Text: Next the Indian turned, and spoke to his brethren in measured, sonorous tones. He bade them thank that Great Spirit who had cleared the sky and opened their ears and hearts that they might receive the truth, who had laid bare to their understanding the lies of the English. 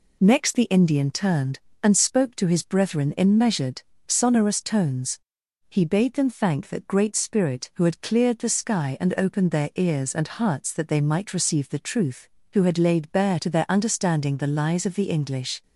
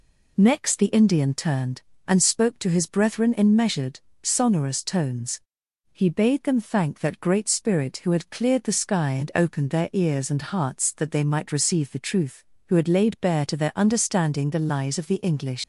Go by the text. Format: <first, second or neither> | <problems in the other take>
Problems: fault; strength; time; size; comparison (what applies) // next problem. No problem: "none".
first | leaves "English" unfinished; at 15.6 s; 85 ms